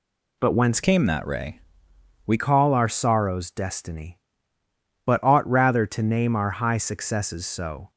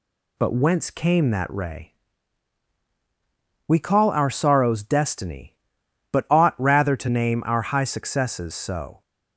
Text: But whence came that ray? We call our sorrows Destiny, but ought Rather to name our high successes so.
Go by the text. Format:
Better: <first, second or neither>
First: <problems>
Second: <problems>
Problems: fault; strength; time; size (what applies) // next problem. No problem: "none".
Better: second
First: changes voice from "came" to "We"; from 0.8 to 2.3 s; 1.5 s long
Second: none